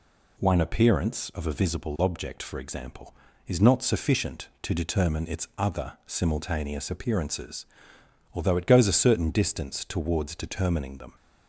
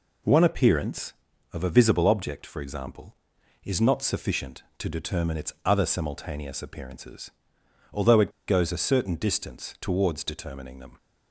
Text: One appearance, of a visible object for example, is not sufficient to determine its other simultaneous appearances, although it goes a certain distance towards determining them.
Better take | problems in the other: first | pauses between "it" and "goes"; slight; at 8.3 s; 0.17 s long

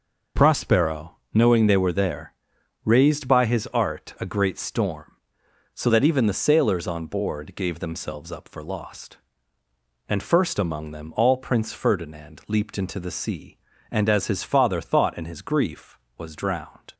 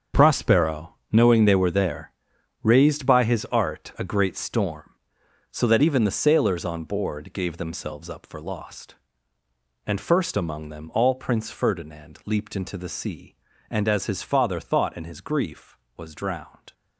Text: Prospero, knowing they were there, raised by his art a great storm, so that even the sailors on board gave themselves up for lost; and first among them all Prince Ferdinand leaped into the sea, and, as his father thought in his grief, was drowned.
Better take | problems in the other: first | gets quieter; strong; throughout; 11.5 dB

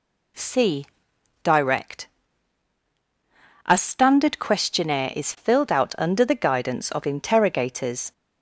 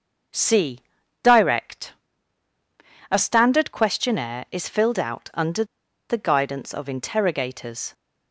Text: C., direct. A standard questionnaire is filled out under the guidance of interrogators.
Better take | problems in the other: first | starts louder than the rest; until 1.7 s; 6.5 dB // pauses between "under" and "the"; at 5.6 s; 0.45 s long

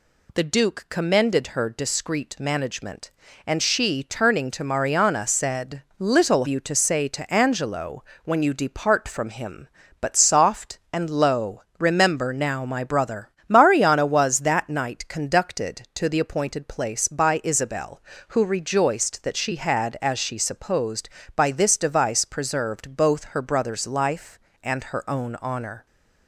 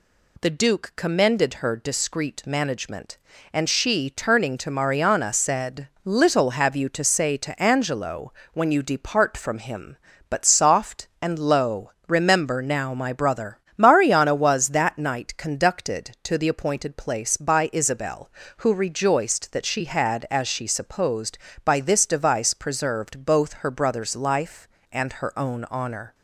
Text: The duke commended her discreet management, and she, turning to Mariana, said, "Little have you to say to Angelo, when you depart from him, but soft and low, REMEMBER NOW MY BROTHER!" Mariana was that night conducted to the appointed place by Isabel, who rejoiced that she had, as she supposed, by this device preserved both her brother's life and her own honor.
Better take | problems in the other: second | skips "have"; at 6.4 s

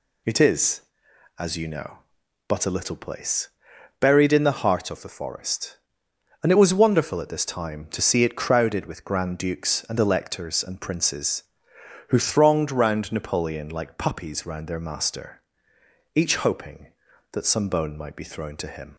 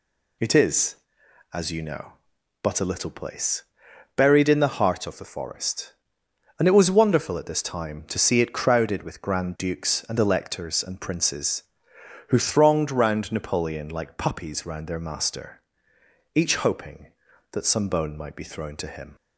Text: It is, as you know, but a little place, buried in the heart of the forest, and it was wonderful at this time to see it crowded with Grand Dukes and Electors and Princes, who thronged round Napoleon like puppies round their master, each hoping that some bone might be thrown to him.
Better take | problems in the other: neither | none

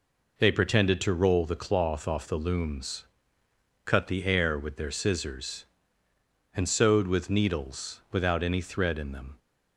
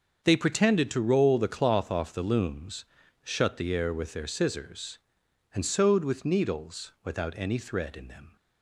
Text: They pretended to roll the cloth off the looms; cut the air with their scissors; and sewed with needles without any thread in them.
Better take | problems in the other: first | starts louder than the rest; until 1.2 s; 6.5 dB // says "shut" for "cut"; at 3.2 s

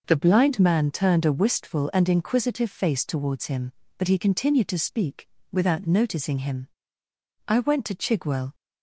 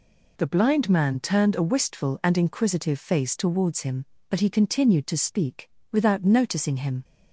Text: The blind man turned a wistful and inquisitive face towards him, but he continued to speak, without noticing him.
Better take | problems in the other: second | goes on to say "I went to Chigwell"; noticeable; from 7.4 s on; 1.0 s long

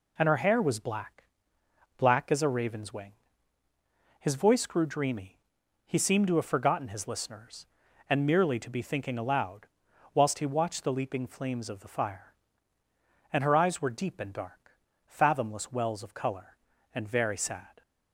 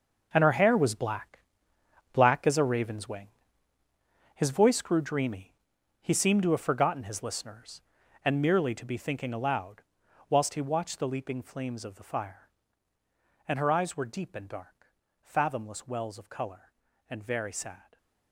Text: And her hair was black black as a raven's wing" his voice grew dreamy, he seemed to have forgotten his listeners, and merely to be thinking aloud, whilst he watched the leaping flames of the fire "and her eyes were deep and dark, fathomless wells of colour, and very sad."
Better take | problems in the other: first | gets quieter; strong; throughout; 14 dB // pauses between "black" and "black"; noticeable; at 1.3 s; 0.74 s long; noticeable in the first // pauses between "wing" and "his"; at 3.2 s; 1.0 s long; also in the first

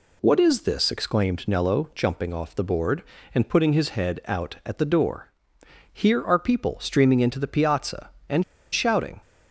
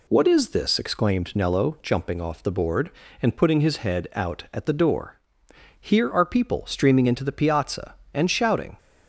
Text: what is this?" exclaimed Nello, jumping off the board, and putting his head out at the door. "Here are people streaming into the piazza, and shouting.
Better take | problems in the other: second | pauses between "and" and "shouting"; slight; at 8.4 s; 0.28 s long

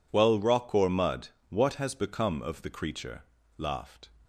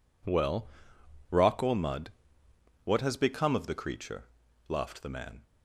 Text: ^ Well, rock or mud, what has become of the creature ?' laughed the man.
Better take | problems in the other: second | stops before "the man"; at 4.2 s

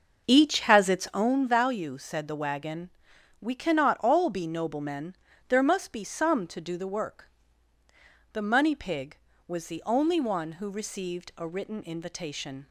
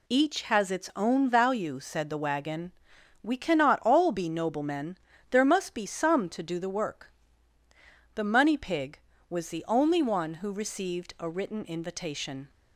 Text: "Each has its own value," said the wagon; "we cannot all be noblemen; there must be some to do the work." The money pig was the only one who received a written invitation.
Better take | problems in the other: second | starts louder than the rest; until 1.3 s; 6 dB

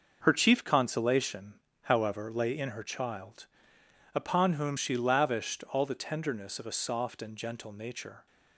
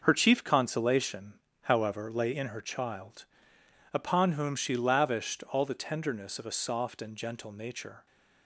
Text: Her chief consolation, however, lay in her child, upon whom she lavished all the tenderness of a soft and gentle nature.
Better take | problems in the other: neither | starts louder than the rest; noticeable; the same in both

